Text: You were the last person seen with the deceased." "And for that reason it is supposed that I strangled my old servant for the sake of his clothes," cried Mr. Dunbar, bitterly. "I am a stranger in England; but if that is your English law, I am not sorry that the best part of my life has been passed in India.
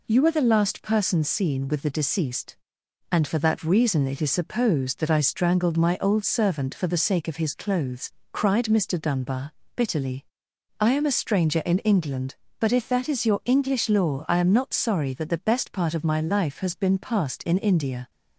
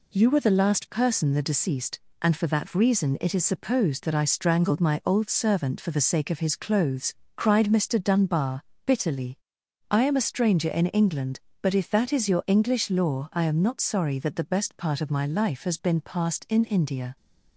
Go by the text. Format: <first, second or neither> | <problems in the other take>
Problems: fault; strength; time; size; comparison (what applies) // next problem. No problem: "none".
first | skips "seen with"; at 1.3 s